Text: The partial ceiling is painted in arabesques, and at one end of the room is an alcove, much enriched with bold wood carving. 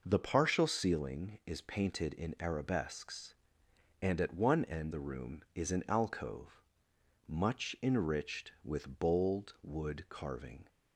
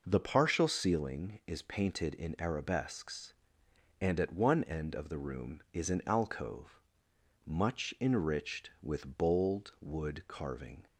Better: second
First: skips "of"; at 4.9 s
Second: none

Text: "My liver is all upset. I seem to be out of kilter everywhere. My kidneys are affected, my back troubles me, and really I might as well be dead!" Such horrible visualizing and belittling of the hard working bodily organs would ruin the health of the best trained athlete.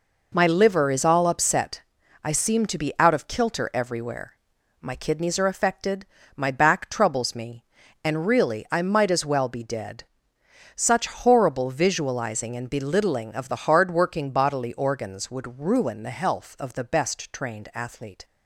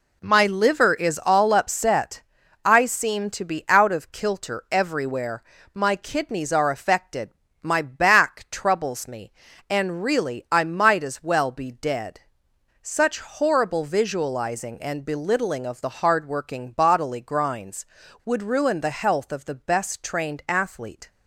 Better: first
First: none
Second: says "grinds" for "organs"; at 17.2 s

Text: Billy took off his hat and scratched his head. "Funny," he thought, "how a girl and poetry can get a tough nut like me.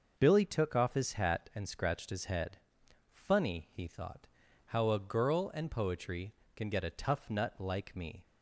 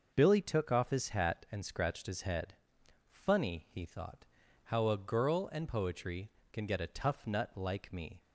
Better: neither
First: none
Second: none

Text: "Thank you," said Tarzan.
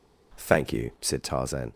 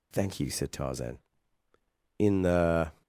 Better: first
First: none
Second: goes on to say "In the"; noticeable; from 2.1 s on; 0.84 s long

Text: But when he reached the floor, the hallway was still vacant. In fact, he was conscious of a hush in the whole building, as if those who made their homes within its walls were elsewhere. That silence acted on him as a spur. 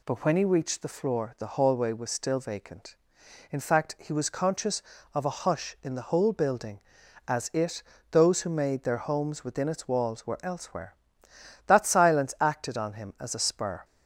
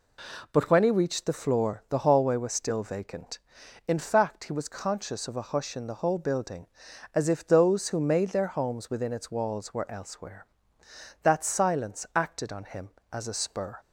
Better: second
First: says "it" for "if"; at 7.5 s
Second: none

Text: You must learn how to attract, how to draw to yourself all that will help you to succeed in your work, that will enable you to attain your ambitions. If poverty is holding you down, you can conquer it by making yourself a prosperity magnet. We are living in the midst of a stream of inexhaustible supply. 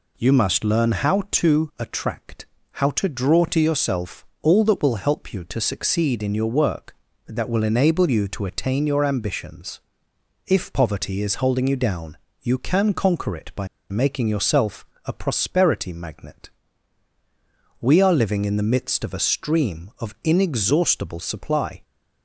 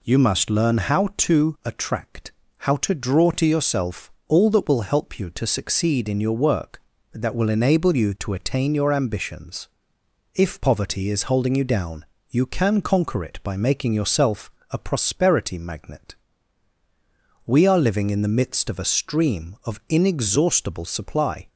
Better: second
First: pauses between "yourself" and "all"; slight; at 4.2 s; 0.18 s long // pauses between "by" and "making"; slight; at 13.6 s; 0.23 s long // pauses between "yourself" and "a"; slight; at 14.8 s; 0.20 s long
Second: pauses between "yourself" and "all"; slight; at 4.1 s; 0.18 s long // pauses between "yourself" and "a"; slight; at 14.5 s; 0.20 s long

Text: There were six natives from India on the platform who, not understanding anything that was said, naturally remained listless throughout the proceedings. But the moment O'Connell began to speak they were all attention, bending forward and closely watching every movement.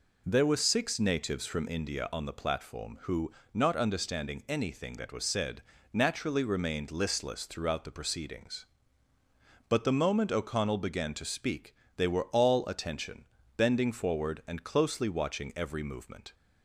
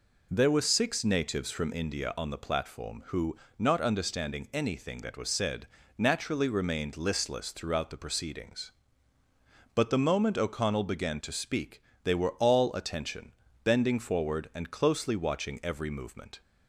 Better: neither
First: pauses between "speak" and "they"; slight; at 11.7 s; 0.22 s long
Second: pauses between "speak" and "they"; slight; at 11.8 s; 0.22 s long

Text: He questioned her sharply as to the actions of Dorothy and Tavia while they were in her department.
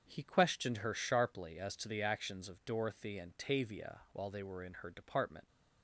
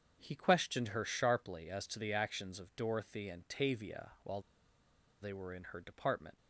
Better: first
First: starts louder than the rest; strong; until 1.1 s; 7.5 dB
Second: starts louder than the rest; strong; until 1.2 s; 7 dB // pauses between "while" and "they"; noticeable; at 4.4 s; 0.79 s long

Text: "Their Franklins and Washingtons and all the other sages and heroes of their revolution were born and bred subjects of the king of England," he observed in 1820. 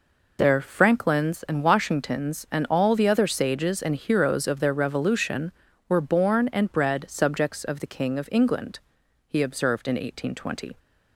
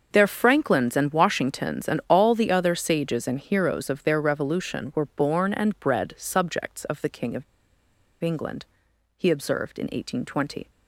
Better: first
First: none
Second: starts louder than the rest; until 1.1 s; 6.5 dB // pauses between "of" and "England"; noticeable; at 7.4 s; 0.79 s long

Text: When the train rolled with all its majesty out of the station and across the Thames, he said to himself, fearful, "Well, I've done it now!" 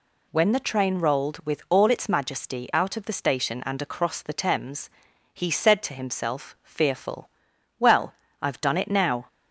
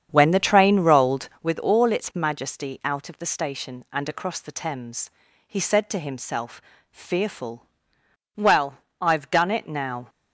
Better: first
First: none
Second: starts louder than the rest; strong; until 1.5 s; 8 dB

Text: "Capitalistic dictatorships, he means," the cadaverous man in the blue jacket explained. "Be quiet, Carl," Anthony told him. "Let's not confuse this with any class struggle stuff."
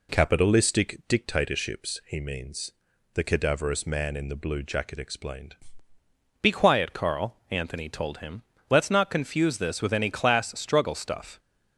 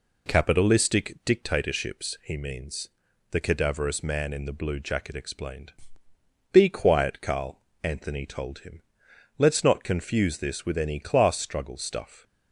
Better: second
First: changes voice at "Be"; from 6.4 s on; 4.9 s long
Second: none

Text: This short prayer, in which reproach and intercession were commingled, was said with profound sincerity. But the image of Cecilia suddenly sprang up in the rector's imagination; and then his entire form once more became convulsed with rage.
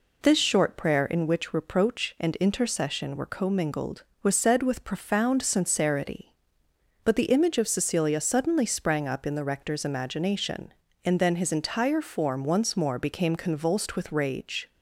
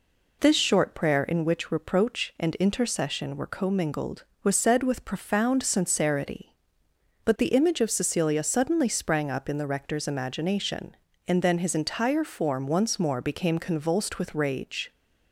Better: neither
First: none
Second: none

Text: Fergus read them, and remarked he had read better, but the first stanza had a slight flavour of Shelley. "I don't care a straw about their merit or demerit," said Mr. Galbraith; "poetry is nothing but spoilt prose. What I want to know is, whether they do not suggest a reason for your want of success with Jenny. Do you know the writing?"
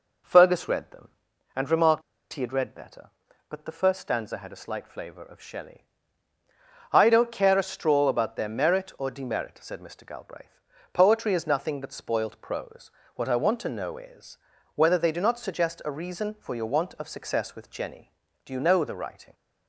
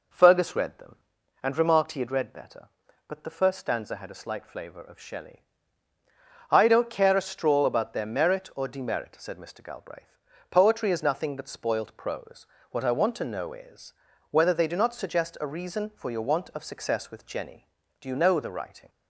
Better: second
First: pauses between "remarked" and "he"; slight; at 2.0 s; 0.31 s long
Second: none

